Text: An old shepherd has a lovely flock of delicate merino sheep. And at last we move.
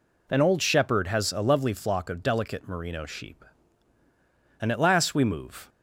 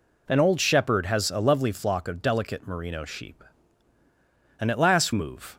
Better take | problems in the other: first | skips "we"; at 5.1 s

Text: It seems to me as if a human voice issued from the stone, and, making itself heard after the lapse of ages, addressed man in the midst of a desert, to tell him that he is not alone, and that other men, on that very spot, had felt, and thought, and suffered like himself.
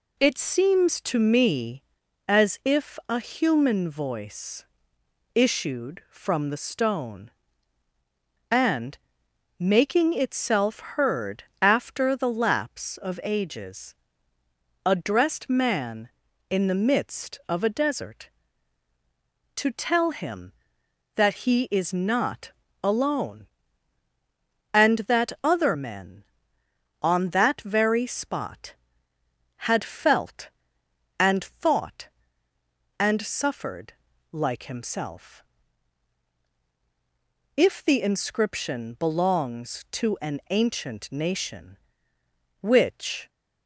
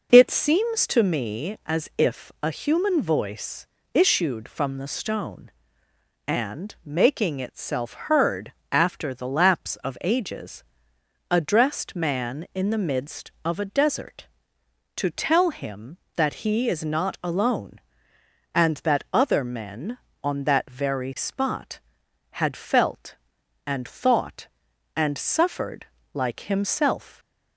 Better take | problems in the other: second | pauses between "voice" and "issued"; noticeable; at 4.6 s; 0.70 s long; slight in the second // pauses between "heard" and "after"; slight; at 11.4 s; 0.18 s long; slight in the second // pauses between "not" and "alone"; slight; at 22.5 s; 0.32 s long // pauses between "suffered" and "like"; slight; at 33.9 s; 0.36 s long; slight in the second // goes on to say "If the inscription belongs to an ancient nation which"; strong; from 37.5 s on; 5.7 s long

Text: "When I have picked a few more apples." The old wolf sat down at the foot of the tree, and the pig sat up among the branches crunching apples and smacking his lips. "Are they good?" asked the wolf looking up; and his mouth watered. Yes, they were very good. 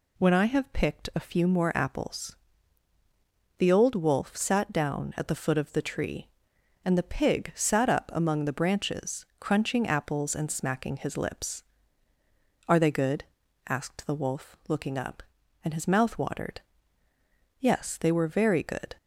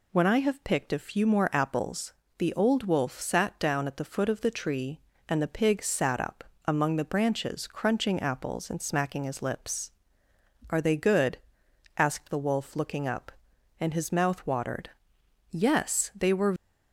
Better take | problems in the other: first | pauses between "up" and "among"; slight; at 6.4 s; 0.22 s long // stops before "very good"; at 16.5 s

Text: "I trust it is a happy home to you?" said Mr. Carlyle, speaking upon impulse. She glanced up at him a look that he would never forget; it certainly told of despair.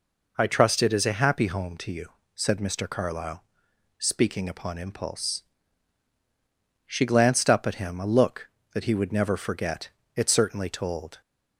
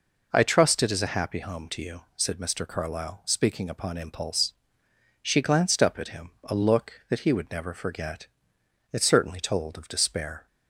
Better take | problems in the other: second | stops before "of despair"; at 11.2 s

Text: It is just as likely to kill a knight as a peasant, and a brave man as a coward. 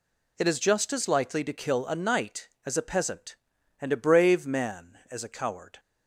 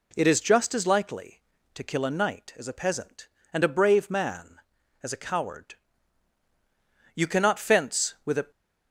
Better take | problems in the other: first | goes on to say "You cannot fence with a"; from 7.1 s on; 1.3 s long

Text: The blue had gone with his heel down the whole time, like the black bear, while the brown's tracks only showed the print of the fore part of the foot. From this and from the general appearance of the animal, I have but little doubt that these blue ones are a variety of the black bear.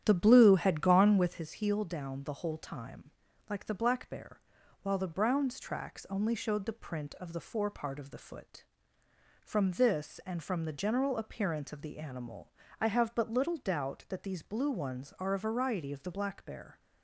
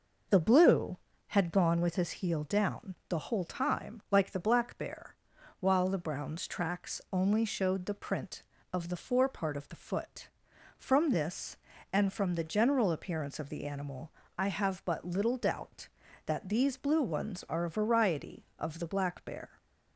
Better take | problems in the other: second | starts louder than the rest; strong; until 1.5 s; 10 dB

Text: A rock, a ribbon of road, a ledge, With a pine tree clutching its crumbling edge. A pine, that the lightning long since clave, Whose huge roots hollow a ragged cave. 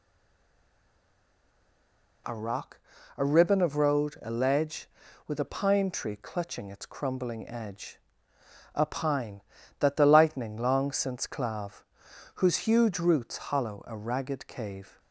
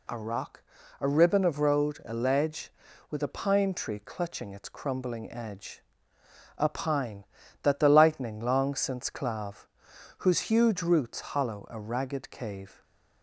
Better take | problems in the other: second | stays silent before the first word; until 2.2 s; 2.2 s long

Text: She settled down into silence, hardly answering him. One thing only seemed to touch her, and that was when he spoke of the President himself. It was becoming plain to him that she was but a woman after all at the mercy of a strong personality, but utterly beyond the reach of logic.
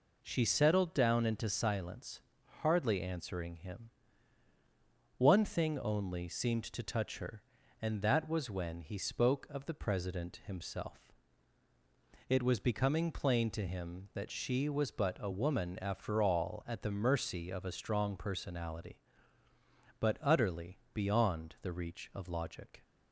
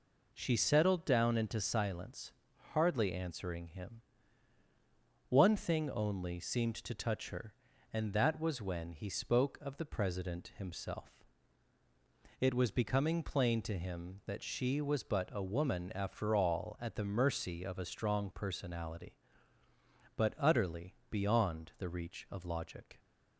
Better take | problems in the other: neither | pauses between "utterly" and "beyond"; slight; the same in both

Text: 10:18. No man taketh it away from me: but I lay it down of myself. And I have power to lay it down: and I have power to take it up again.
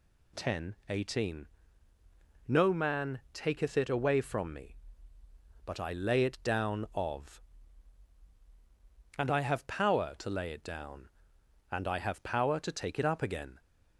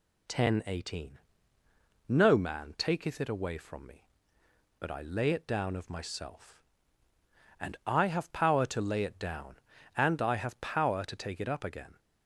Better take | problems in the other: second | skips "myself"; at 8.2 s

